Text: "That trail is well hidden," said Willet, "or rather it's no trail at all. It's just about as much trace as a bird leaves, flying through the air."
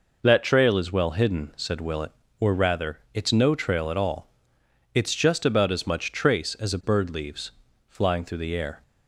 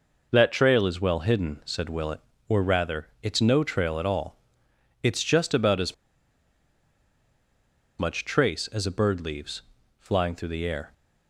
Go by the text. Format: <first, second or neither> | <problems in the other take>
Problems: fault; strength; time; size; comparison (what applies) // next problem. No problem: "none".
first | pauses between "rather" and "it's"; slight; at 3.0 s; 0.16 s long; slight in the first // pauses between "as" and "much"; strong; at 5.9 s; 2.0 s long